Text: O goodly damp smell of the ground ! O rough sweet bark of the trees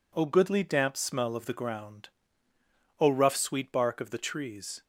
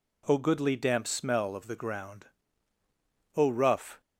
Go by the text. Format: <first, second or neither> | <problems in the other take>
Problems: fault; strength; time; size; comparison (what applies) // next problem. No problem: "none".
first | stops before "sweet bark of the trees"; at 4.0 s